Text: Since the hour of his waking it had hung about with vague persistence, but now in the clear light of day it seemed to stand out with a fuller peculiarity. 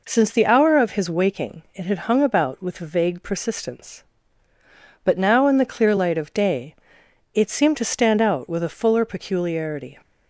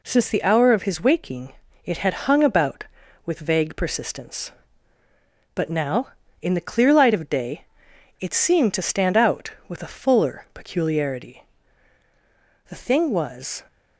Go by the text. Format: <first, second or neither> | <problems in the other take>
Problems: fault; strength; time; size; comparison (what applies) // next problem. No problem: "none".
first | pauses between "waking" and "it"; slight; at 1.5 s; 0.32 s long // pauses between "day" and "it"; noticeable; at 7.6 s; 0.56 s long; noticeable in the first // goes on to say "The thing was"; noticeable; from 12.6 s on; 0.96 s long